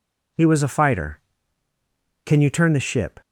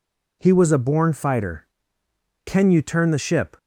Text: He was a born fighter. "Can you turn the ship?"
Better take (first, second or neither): second